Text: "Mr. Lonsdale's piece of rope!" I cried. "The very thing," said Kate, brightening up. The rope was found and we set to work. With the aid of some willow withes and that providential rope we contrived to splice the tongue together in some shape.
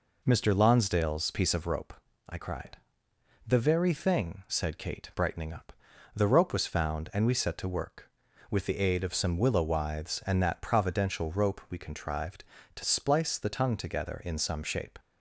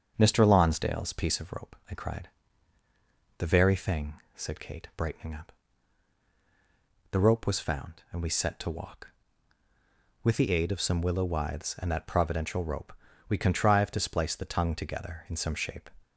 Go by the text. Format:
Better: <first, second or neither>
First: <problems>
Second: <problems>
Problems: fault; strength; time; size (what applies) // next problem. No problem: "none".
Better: first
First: none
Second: starts louder than the rest; until 1.1 s; 7 dB // says "walk" for "work"; at 8.7 s // pauses between "rope" and "we"; slight; at 12.9 s; 0.34 s long